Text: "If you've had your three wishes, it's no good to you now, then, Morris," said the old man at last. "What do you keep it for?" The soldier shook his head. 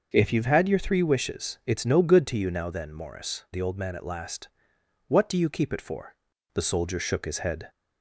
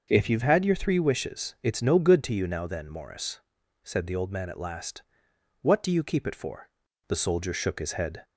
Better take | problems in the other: second | starts louder than the rest; until 1.1 s; 6.5 dB; also in the second // skips "said"; at 3.4 s

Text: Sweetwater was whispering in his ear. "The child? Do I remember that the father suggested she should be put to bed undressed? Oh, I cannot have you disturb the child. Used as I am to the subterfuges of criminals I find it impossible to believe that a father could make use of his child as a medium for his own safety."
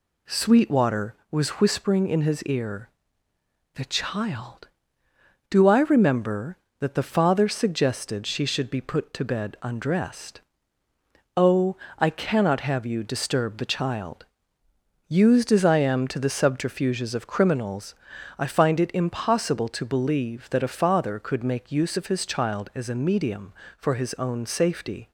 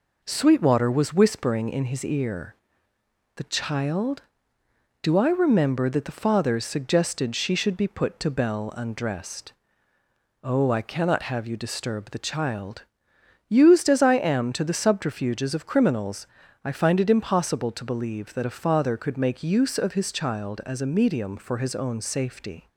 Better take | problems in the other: first | says "bell" for "bed"; at 8.2 s // pauses between "criminals" and "I"; slight; at 16.2 s; 0.36 s long; also in the first

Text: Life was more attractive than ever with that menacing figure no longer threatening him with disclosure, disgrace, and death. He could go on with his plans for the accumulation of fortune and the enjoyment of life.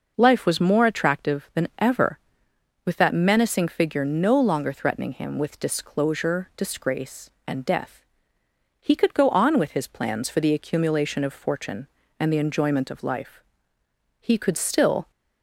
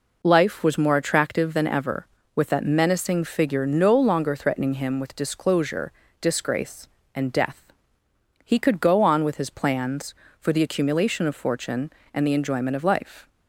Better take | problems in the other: second | goes on to say "He could still"; noticeable; from 14.1 s on; 0.92 s long

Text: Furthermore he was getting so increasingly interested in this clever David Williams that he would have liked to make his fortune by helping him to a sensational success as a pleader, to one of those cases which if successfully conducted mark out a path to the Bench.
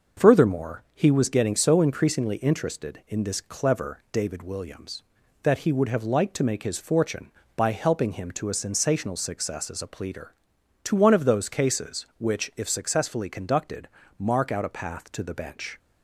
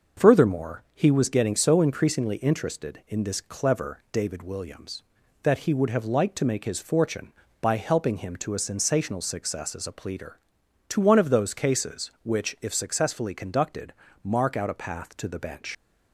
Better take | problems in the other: first | starts louder than the rest; until 1.3 s; 6 dB; also in the first // pauses between "conducted" and "mark"; slight; at 13.9 s; 0.30 s long; slight in the first // leaves "Bench" unfinished; at 15.7 s; 85 ms

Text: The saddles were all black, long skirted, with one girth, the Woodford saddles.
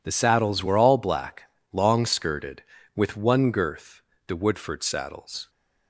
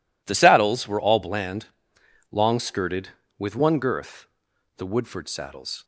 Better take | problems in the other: first | says "bland" for "black"; at 1.2 s

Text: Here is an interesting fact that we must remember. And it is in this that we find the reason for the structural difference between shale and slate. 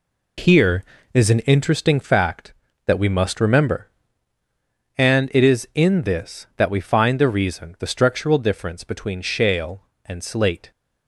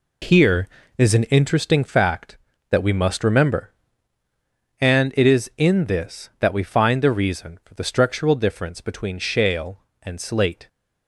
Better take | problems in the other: second | skips "for"; at 7.7 s

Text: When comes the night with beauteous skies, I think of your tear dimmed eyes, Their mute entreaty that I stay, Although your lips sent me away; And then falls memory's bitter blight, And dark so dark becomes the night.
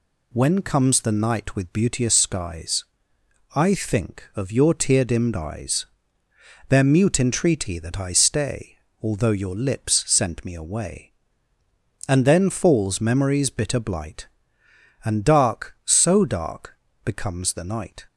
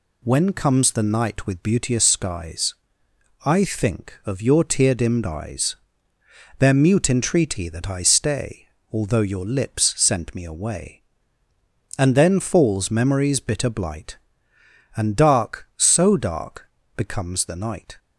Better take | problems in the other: neither | pauses between "dark" and "becomes"; slight; the same in both

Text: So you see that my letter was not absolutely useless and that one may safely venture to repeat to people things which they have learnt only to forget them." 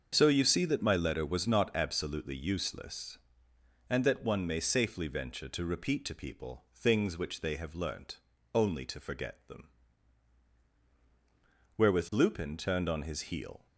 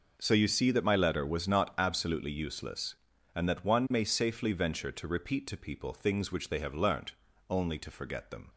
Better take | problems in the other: second | starts louder than the rest; until 1.1 s; 6.5 dB // pauses between "learnt" and "only"; slight; at 8.1 s; 0.34 s long; also in the second // goes on to say "Wherewith Lupin turned on his heel"; strong; from 11.7 s on; 1.8 s long

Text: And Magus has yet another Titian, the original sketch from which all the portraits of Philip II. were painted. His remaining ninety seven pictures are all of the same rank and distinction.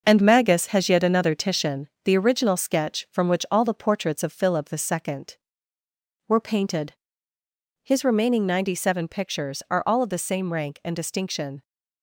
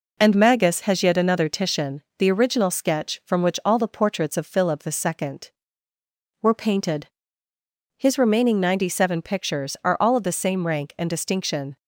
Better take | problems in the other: second | gets quieter; noticeable; throughout; 6 dB

